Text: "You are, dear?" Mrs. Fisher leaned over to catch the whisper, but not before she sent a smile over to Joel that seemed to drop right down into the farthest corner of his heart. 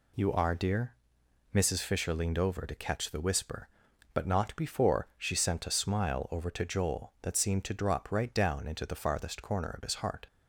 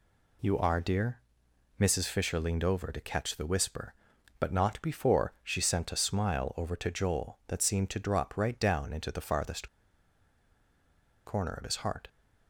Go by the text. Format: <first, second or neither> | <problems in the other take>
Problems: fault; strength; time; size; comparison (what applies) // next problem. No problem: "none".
first | pauses between "farthest" and "corner"; strong; at 9.6 s; 1.5 s long